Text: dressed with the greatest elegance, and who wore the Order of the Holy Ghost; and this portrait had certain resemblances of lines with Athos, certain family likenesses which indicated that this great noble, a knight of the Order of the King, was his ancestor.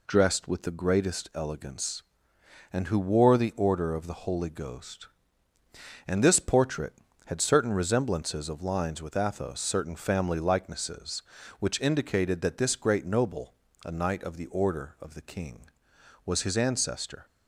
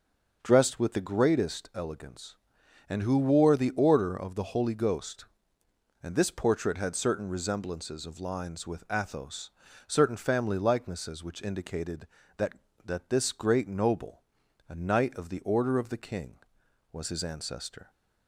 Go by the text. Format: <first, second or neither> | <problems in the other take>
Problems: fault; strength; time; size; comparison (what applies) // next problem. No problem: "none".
first | starts louder than the rest; noticeable; until 1.4 s; 6 dB // says "that" twice; at 12.8 s